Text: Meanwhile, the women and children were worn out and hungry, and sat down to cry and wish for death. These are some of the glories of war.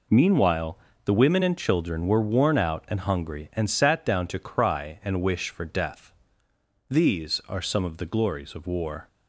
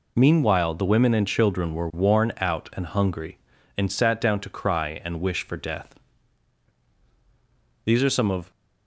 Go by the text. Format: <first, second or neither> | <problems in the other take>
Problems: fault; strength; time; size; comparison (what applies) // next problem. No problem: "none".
first | stops before "the glories of war"; at 8.5 s